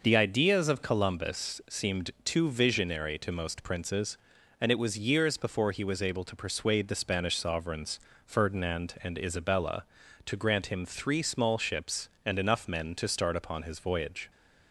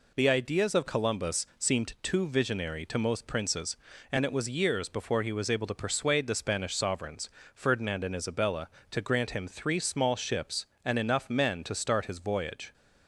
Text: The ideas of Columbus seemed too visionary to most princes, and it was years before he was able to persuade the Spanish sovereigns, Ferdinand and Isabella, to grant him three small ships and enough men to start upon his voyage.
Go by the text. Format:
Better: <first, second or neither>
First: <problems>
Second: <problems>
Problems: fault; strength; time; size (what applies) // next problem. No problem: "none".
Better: first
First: none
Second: skips "upon"; at 12.0 s